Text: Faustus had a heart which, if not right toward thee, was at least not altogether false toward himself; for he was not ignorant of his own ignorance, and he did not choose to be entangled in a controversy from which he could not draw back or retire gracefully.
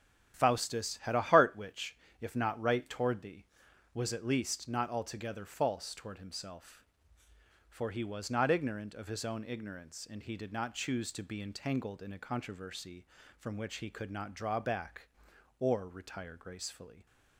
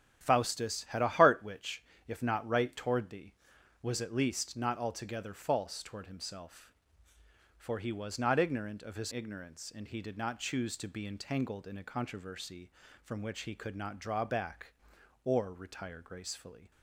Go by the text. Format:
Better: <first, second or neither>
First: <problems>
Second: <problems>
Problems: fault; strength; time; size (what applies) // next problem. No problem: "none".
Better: first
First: starts louder than the rest; strong; until 1.3 s; 10 dB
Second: starts louder than the rest; strong; until 1.2 s; 10 dB // skips "own"; at 9.1 s